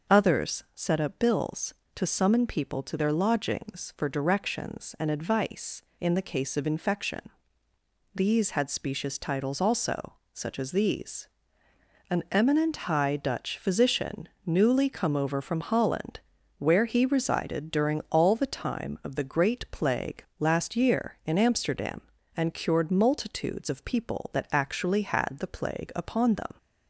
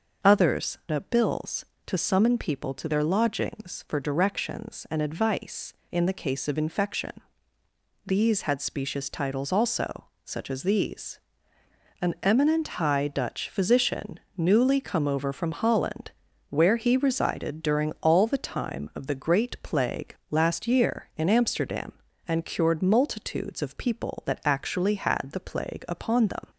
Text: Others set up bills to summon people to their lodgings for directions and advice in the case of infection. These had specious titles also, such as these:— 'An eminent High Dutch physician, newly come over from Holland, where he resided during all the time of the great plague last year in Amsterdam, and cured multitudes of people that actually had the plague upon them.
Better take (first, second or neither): first